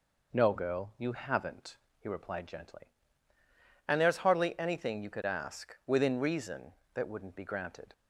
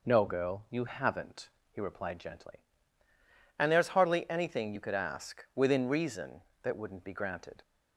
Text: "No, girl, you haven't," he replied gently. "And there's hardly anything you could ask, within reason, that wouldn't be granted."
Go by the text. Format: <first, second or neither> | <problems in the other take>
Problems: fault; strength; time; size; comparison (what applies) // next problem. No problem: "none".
neither | none